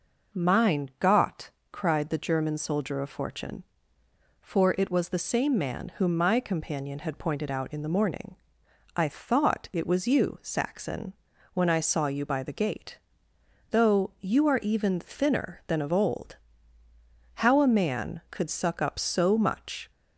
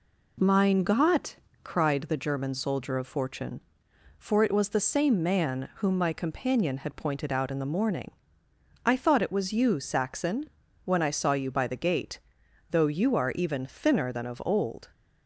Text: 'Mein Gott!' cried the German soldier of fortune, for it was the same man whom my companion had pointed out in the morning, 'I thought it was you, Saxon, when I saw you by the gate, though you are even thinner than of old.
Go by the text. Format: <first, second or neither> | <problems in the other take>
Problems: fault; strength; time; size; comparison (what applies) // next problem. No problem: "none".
second | goes on to say "How a man could suck up so much"; strong; from 17.3 s on; 2.5 s long